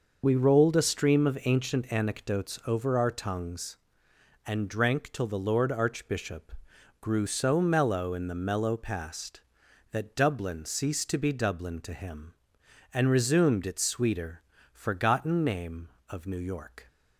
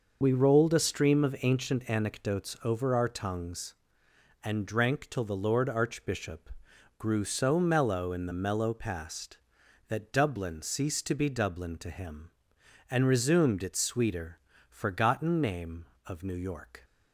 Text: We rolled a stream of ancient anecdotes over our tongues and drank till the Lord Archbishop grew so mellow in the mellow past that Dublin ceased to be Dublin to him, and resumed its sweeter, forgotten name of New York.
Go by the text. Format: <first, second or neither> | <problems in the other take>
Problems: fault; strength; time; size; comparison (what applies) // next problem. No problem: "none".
neither | pauses between "Archbishop" and "grew"; noticeable; the same in both